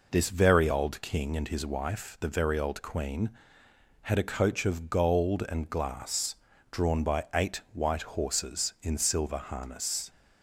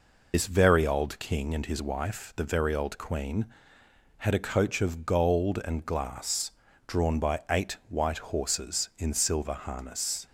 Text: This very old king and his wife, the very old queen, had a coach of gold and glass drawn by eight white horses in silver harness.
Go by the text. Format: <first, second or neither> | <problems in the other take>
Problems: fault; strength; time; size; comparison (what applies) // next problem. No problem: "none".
first | loses the start of "This"; at 0.3 s; 65 ms // pauses between "glass" and "drawn"; at 6.4 s; 0.38 s long; also in the first